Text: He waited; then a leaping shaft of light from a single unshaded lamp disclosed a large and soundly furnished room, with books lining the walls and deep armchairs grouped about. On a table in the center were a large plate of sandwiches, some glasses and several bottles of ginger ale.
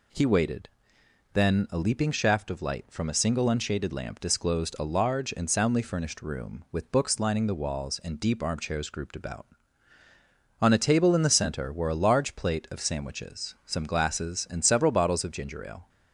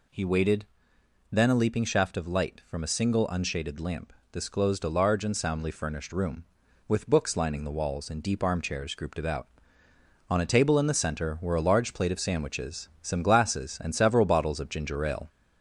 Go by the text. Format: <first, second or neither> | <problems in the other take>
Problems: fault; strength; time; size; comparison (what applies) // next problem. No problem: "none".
first | gets louder; slight; throughout; 2.5 dB // pauses between "lamp" and "disclosed"; slight; at 4.1 s; 0.20 s long